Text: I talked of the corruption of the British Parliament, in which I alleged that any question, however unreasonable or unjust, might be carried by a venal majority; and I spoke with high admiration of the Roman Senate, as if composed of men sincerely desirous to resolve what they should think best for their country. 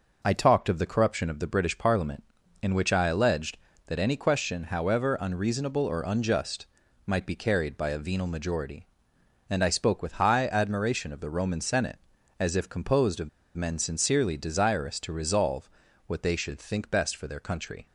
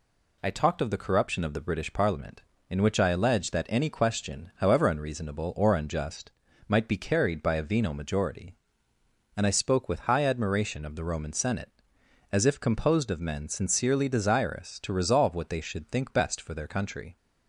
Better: second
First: pauses between "of" and "men"; slight; at 13.2 s; 0.28 s long // pauses between "resolve" and "what"; at 15.6 s; 0.38 s long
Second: none

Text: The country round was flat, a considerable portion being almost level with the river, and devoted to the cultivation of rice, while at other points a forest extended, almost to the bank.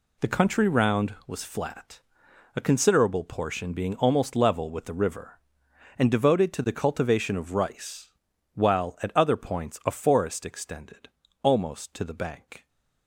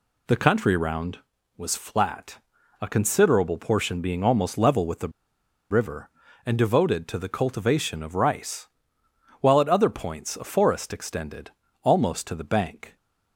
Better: first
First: none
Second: pauses between "the" and "river"; noticeable; at 5.0 s; 0.61 s long

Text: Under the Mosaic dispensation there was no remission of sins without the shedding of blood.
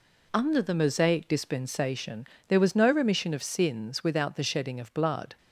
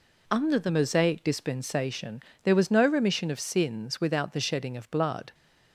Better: neither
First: pauses between "dispensation" and "there"; slight; at 2.2 s; 0.24 s long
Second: pauses between "dispensation" and "there"; slight; at 2.1 s; 0.24 s long

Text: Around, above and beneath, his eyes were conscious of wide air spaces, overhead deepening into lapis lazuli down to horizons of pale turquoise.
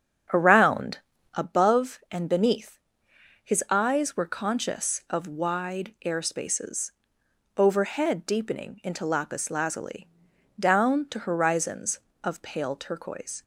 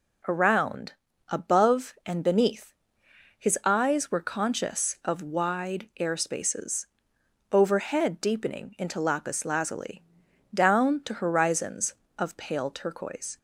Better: second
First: starts louder than the rest; strong; until 1.4 s; 8.5 dB // pauses between "lazuli" and "down"; noticeable; at 10.0 s; 0.50 s long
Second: pauses between "lazuli" and "down"; noticeable; at 10.0 s; 0.50 s long

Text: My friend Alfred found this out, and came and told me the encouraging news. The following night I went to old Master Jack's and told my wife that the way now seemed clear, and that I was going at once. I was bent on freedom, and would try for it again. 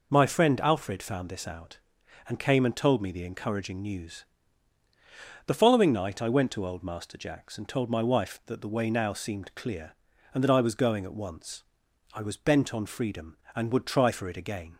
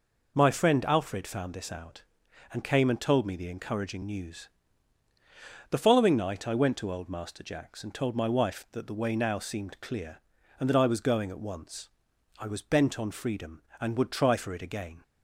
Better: neither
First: none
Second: none

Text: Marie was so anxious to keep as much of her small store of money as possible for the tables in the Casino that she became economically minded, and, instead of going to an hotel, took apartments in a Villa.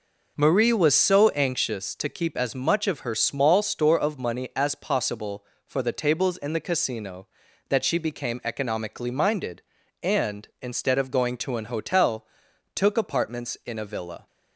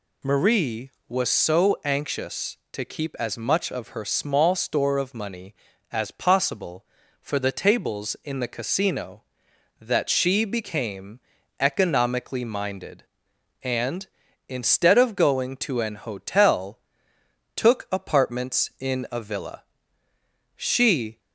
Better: first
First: none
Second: pauses between "became" and "economically"; at 11.1 s; 0.40 s long // goes on to say "She"; noticeable; from 20.5 s on; 0.62 s long

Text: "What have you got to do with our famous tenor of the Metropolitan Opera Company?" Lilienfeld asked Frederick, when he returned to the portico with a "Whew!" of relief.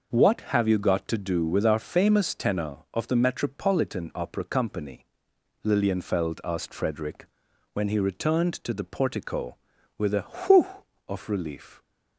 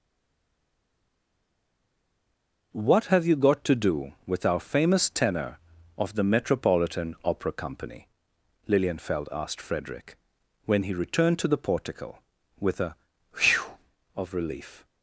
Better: first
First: none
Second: stays silent before the first word; strong; until 2.7 s; 2.7 s long // pauses between "a" and "Whew"; at 12.9 s; 0.42 s long

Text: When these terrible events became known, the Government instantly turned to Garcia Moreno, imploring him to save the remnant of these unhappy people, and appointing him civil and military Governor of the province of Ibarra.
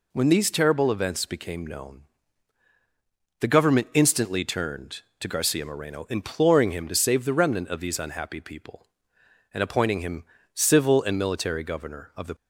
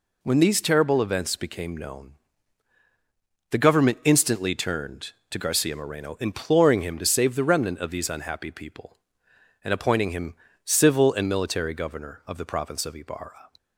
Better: second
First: pauses between "him" and "civil"; slight; at 10.2 s; 0.30 s long // stops before "province of Ibarra"; at 12.3 s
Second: pauses between "him" and "civil"; slight; at 10.3 s; 0.30 s long

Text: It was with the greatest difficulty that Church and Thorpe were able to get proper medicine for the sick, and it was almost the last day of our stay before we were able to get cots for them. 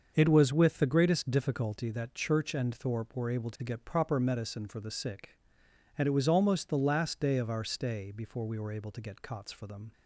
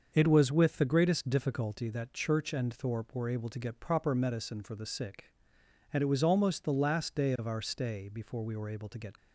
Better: first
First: starts louder than the rest; until 1.1 s; 6.5 dB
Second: starts louder than the rest; until 1.1 s; 6.5 dB // stops before "cots for them"; at 9.1 s

